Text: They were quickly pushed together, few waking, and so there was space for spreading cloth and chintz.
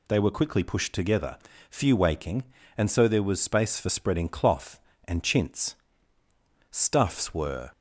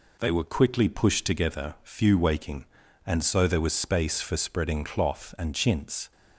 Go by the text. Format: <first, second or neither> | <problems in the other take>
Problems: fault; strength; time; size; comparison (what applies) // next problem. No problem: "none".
second | goes on to say "Stuffs were"; noticeable; from 6.7 s on; 1.0 s long